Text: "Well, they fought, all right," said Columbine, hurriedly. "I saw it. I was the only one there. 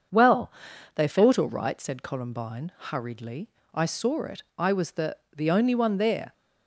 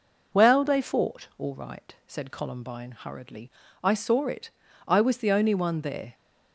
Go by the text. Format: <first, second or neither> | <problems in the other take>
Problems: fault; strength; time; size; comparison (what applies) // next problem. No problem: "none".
second | starts louder than the rest; until 1.5 s; 7 dB // says "the" twice; at 5.3 s